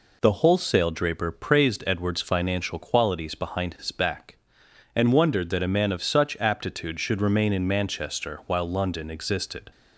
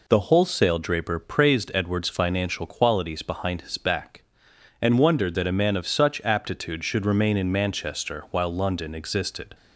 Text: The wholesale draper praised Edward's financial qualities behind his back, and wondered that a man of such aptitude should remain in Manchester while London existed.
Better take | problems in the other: neither | none

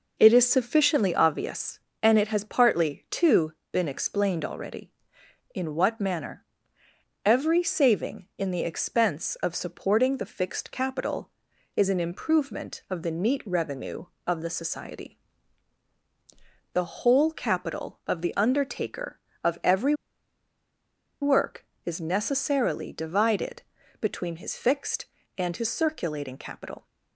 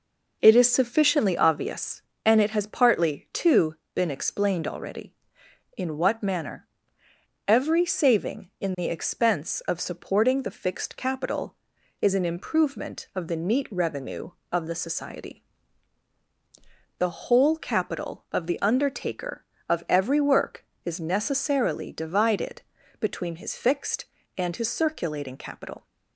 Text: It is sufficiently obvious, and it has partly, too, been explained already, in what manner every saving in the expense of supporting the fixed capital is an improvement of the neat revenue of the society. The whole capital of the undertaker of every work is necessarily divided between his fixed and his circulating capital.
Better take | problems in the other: second | pauses between "manner" and "every"; noticeable; at 6.4 s; 0.80 s long; noticeable in the second // pauses between "every" and "work"; strong; at 19.9 s; 1.2 s long // pauses between "divided" and "between"; at 23.6 s; 0.38 s long; also in the second

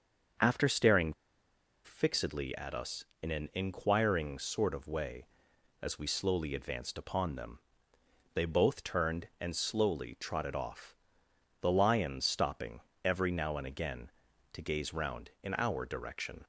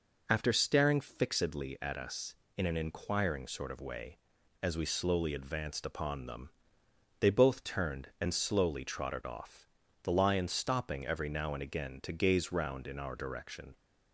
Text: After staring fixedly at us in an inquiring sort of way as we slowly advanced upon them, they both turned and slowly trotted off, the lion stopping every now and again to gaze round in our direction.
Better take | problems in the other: second | starts louder than the rest; until 2.1 s; 6.5 dB // pauses between "staring" and "fixedly"; noticeable; at 1.1 s; 0.71 s long // pauses between "stopping" and "every"; slight; at 12.8 s; 0.24 s long

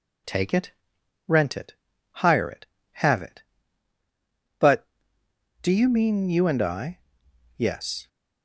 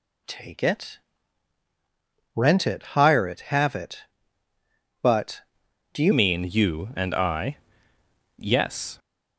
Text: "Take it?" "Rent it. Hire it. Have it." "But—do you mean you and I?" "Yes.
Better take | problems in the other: first | changes voice at "mean"; from 6.1 s on; 2.8 s long

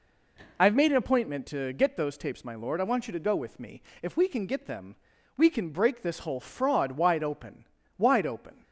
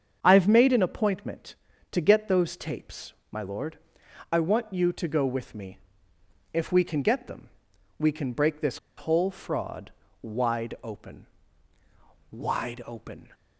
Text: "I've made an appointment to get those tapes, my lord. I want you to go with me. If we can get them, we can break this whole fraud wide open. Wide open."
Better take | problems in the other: first | starts louder than the rest; strong; until 1.2 s; 7 dB // pauses between "this" and "whole"; slight; at 8.7 s; 0.21 s long // pauses between "fraud" and "wide"; slight; at 9.9 s; 0.32 s long

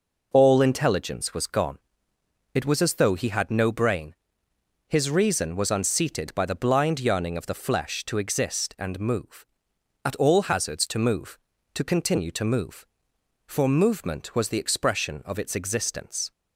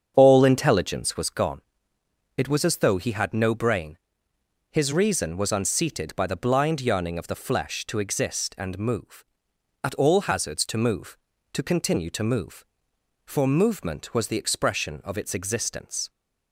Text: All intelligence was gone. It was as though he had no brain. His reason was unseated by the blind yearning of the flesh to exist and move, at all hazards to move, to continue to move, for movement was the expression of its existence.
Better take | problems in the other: first | starts louder than the rest; strong; until 1.3 s; 7.5 dB

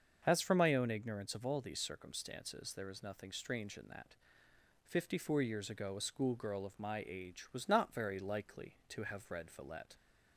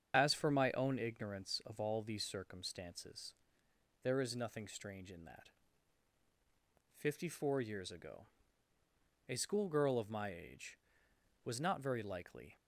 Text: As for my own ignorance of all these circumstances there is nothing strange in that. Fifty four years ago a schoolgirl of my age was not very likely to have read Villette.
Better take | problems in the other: first | starts louder than the rest; strong; until 1.1 s; 7.5 dB; also in the first // pauses between "circumstances" and "there"; noticeable; at 3.3 s; 0.68 s long // pauses between "ago" and "a"; at 8.2 s; 1.0 s long // stops before "to have read Villette"; at 12.5 s

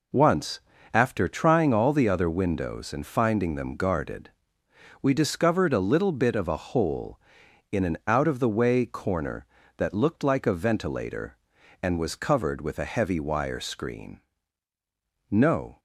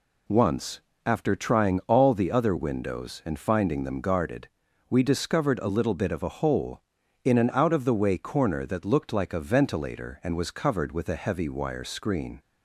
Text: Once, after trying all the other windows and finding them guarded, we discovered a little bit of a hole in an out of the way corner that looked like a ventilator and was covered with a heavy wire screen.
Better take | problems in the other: second | goes on to say "No"; from 15.2 s on; 0.50 s long

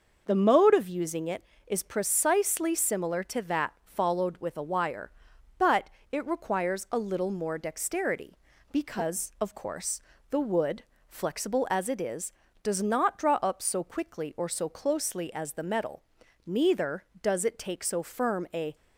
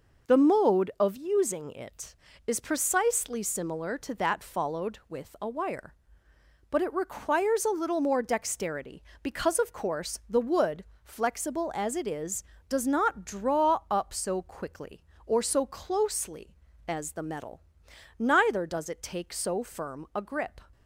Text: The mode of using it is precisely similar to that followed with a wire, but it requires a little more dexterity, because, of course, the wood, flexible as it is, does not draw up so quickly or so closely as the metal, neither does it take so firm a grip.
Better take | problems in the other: second | pauses between "but" and "it"; slight; at 5.8 s; 0.22 s long // stops before "grip"; at 18.7 s

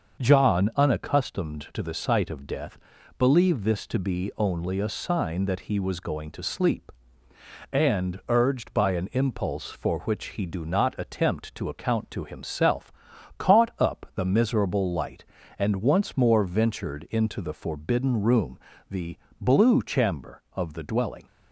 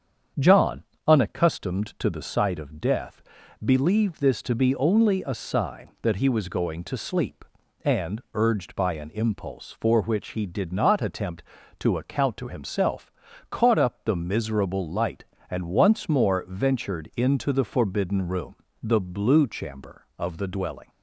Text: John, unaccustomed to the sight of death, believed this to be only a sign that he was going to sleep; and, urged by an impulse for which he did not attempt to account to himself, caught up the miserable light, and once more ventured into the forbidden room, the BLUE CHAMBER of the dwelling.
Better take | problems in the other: second | starts louder than the rest; until 1.2 s; 6.5 dB; strong in the second // says "do" for "did"; at 10.4 s // pauses between "the" and "BLUE"; slight; at 19.1 s; 0.24 s long

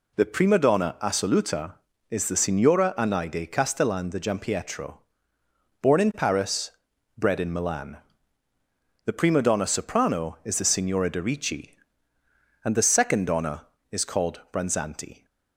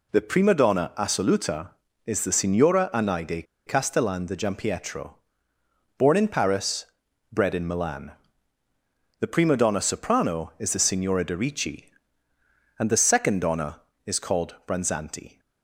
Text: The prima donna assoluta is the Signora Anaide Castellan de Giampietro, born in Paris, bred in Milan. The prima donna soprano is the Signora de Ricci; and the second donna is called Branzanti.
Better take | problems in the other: first | pauses between "Anaide" and "Castellan"; slight; at 3.4 s; 0.21 s long

